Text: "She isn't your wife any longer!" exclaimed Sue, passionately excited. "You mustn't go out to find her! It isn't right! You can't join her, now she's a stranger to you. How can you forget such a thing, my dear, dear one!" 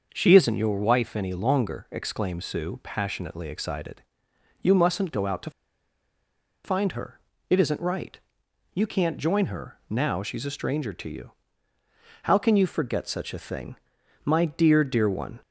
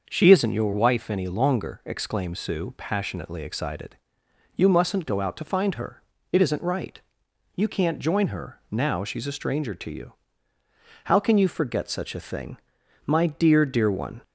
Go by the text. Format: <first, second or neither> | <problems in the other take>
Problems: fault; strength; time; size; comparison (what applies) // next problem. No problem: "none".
second | starts louder than the rest; until 1.1 s; 6.5 dB; also in the second // pauses between "to" and "find"; at 5.5 s; 1.1 s long